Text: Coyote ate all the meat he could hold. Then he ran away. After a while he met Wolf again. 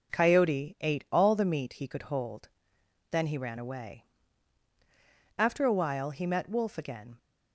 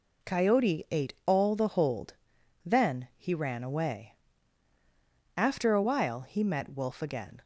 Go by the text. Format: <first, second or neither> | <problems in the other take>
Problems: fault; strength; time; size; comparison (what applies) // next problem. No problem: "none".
first | skips "meat he could"; at 1.6 s